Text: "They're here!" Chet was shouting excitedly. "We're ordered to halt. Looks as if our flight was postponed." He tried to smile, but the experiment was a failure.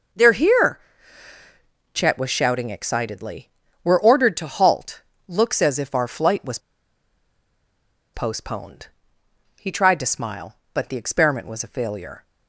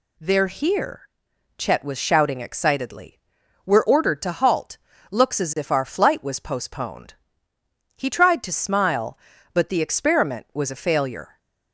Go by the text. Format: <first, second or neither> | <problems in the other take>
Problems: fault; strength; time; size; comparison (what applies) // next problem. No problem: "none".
second | starts louder than the rest; noticeable; until 2.3 s; 6 dB // pauses between "was" and "postponed"; strong; at 6.5 s; 1.5 s long